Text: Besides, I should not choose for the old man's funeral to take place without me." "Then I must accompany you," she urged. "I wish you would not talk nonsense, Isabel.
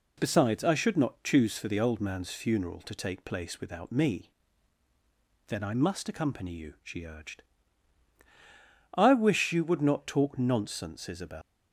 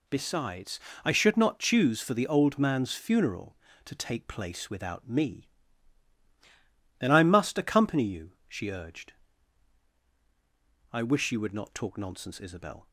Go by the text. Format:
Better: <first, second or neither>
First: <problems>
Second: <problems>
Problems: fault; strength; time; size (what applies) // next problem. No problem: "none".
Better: second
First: leaves "Isabel" unfinished; at 11.4 s; 165 ms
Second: none